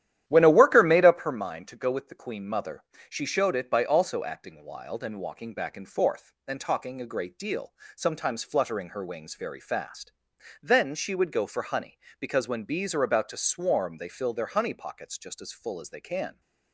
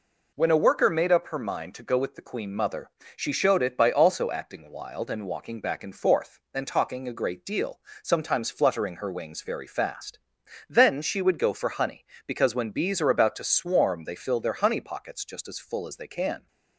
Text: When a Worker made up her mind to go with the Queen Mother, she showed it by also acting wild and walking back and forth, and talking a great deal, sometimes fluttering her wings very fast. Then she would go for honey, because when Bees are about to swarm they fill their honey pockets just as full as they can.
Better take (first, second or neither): second